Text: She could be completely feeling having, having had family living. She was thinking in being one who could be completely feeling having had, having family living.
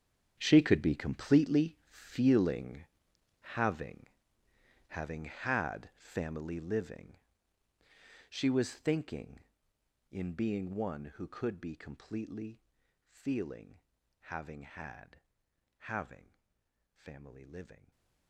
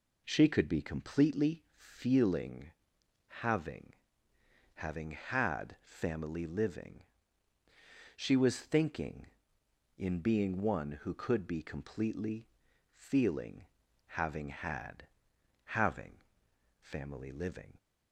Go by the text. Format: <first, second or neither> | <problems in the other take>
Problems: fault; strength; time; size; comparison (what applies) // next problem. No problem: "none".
second | gets quieter; strong; throughout; 16.5 dB // pauses between "feeling" and "having"; noticeable; at 2.8 s; 0.56 s long; noticeable in the second // pauses between "completely" and "feeling"; at 12.6 s; 0.44 s long; also in the second // pauses between "feeling" and "having"; at 13.7 s; 0.42 s long; also in the second // pauses between "having" and "family"; noticeable; at 16.3 s; 0.64 s long; noticeable in the second // stays silent after the last word; slight; from 17.7 s on; 0.5 s long